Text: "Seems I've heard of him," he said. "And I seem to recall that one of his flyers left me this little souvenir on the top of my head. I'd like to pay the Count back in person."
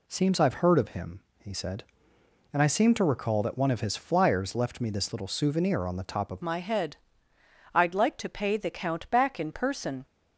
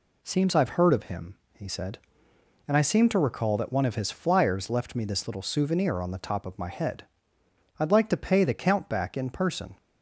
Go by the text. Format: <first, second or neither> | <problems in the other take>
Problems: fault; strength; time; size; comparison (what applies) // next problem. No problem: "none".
second | changes voice at "my"; from 6.4 s on; 3.6 s long